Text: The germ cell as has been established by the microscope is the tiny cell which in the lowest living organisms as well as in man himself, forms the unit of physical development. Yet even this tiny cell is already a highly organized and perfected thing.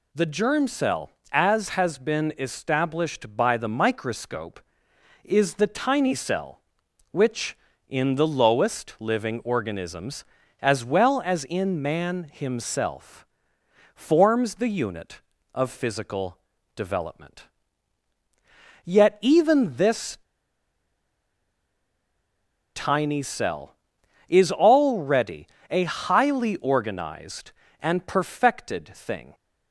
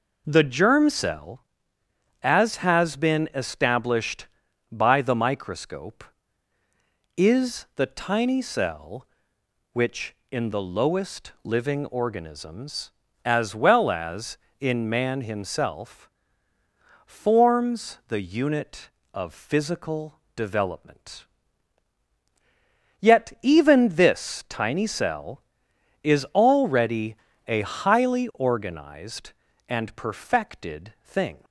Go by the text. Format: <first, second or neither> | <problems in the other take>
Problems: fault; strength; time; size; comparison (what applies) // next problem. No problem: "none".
second | pauses between "physical" and "development"; at 16.3 s; 0.38 s long; slight in the second // pauses between "this" and "tiny"; strong; at 20.1 s; 2.5 s long // pauses between "already" and "a"; slight; at 25.4 s; 0.24 s long; slight in the second